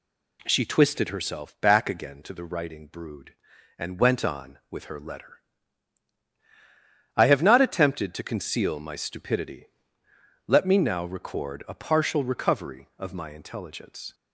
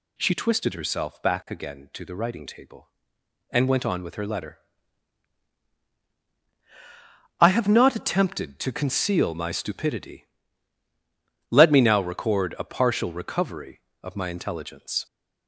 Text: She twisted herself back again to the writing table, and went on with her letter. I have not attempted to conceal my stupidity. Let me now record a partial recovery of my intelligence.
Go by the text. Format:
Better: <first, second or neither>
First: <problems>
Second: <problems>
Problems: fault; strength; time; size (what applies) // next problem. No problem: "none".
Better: second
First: says "brood" for "table"; at 2.8 s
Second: none